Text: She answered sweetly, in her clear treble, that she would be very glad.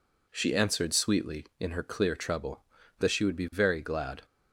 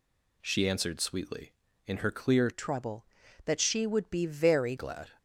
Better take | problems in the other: first | changes voice from "treble" to "very"; from 2.5 to 4.7 s; 2.2 s long

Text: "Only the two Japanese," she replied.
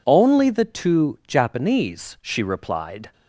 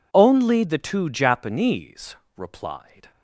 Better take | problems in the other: first | skips "she"; at 2.2 s

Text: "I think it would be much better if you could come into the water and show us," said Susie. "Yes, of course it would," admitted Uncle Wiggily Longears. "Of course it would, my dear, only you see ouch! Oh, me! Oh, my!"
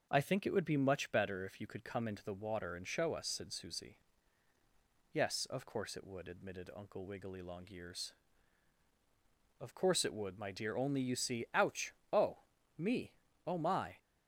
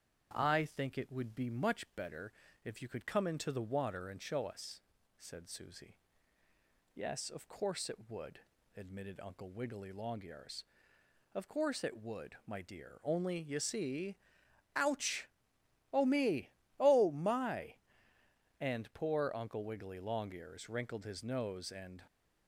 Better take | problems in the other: first | starts louder than the rest; strong; until 1.3 s; 8 dB; noticeable in the first // pauses between "better" and "if"; slight; at 2.3 s; 0.32 s long // pauses between "see" and "ouch"; noticeable; at 14.1 s; 0.58 s long // goes on to say "and poor Uncle Wiggily Longears wrinkled his nose and"; strong; from 18.5 s on; 3.4 s long

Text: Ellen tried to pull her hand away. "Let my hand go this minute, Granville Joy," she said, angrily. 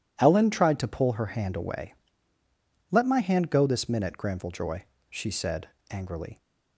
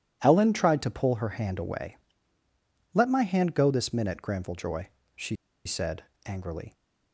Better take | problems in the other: first | pauses between "she" and "said"; slight; at 5.3 s; 0.29 s long

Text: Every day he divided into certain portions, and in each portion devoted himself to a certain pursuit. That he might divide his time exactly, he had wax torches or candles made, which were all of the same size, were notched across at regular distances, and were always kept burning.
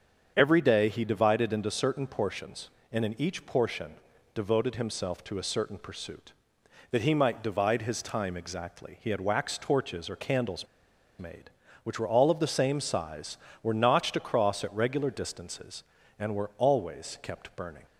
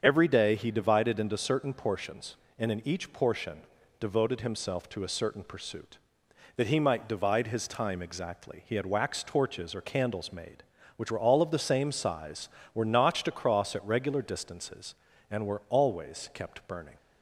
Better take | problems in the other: second | starts louder than the rest; strong; until 1.3 s; 7.5 dB; strong in the second // pauses between "portion" and "devoted"; at 3.9 s; 0.40 s long; also in the second // pauses between "candles" and "made"; noticeable; at 10.6 s; 0.52 s long

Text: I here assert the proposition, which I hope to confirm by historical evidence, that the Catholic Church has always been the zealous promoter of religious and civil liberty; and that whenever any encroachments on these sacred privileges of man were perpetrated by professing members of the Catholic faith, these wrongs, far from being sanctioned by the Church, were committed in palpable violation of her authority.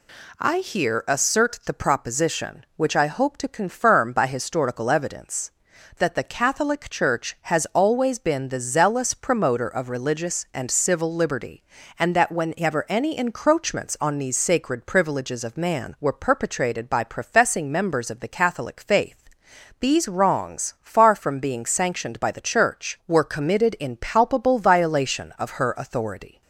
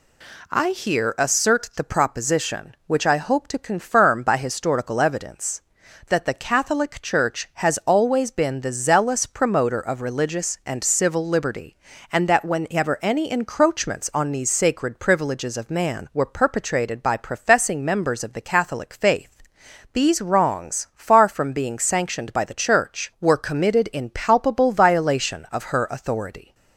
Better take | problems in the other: neither | none

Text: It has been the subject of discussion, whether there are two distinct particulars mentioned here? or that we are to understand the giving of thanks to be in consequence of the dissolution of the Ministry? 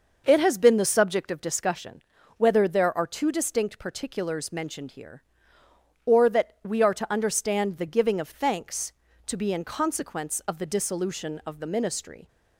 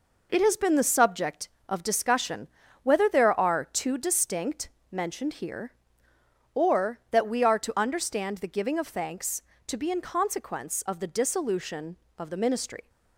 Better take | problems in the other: first | skips "particulars"; at 4.7 s

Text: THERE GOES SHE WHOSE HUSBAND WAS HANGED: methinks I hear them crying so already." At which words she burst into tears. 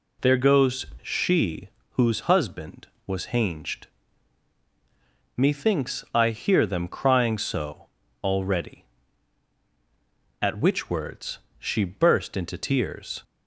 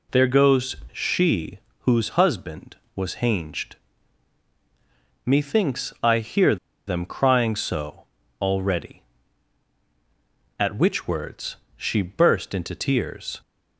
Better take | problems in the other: first | pauses between "GOES" and "SHE"; slight; at 0.7 s; 0.16 s long; slight in the first // pauses between "SHE" and "WHOSE"; slight; at 1.5 s; 0.22 s long; slight in the first // pauses between "hear" and "them"; slight; at 6.5 s; 0.31 s long // pauses between "so" and "already"; slight; at 8.0 s; 0.36 s long; slight in the first // pauses between "words" and "she"; slight; at 11.5 s; 0.18 s long; slight in the first

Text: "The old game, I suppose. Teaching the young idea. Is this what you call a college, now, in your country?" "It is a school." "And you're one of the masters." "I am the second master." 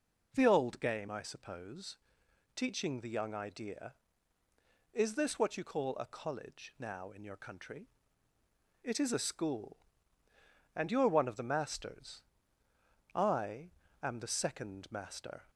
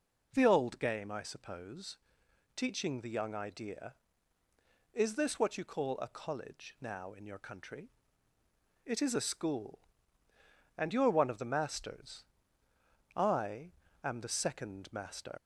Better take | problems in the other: first | pauses between "I" and "am"; slight; at 13.7 s; 0.30 s long; slight in the first // leaves "master" unfinished; at 15.3 s; 130 ms

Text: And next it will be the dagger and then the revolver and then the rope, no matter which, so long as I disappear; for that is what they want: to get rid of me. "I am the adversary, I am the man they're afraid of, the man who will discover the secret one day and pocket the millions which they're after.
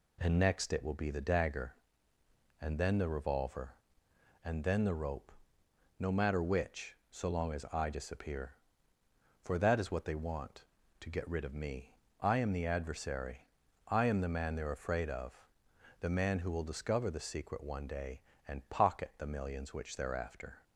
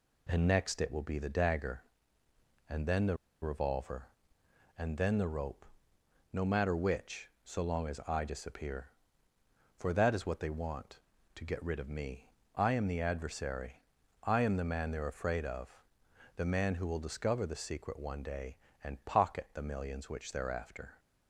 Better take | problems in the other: first | pauses between "the" and "revolver"; slight; at 3.1 s; 0.26 s long

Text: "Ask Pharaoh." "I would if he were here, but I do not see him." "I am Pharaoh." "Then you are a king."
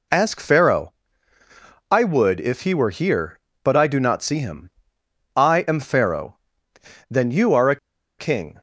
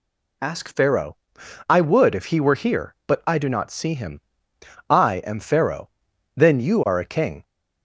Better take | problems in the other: second | pauses between "a" and "king"; at 7.7 s; 0.42 s long

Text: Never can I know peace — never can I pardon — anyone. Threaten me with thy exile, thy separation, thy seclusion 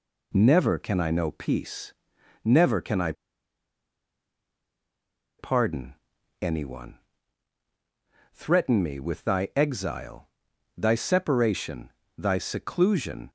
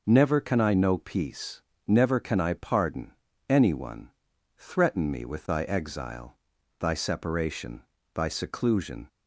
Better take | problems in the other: second | pauses between "I" and "pardon"; strong; at 3.1 s; 2.2 s long

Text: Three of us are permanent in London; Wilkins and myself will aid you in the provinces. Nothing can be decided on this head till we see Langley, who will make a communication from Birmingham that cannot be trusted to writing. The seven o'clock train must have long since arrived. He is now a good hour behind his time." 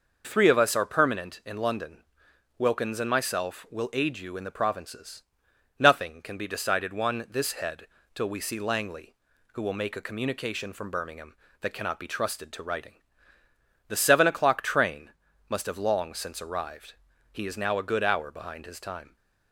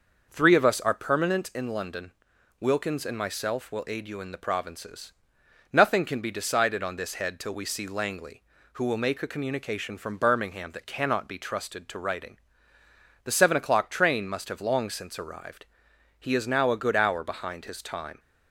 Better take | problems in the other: second | says "one" for "on"; at 6.9 s // pauses between "head" and "till"; slight; at 7.8 s; 0.28 s long // pauses between "train" and "must"; slight; at 15.1 s; 0.36 s long

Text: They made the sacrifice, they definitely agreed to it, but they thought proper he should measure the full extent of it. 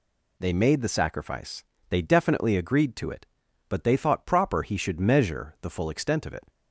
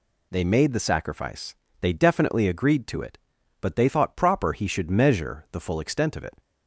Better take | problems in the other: neither | none

